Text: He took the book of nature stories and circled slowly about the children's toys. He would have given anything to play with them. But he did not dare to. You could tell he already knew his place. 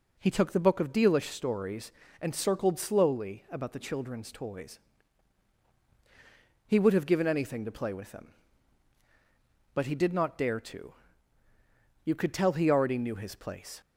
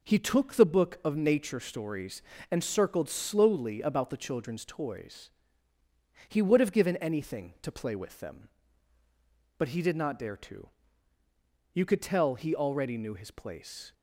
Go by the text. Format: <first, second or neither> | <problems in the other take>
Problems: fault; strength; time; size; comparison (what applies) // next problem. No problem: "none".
second | says "dealish" for "nature"; at 0.9 s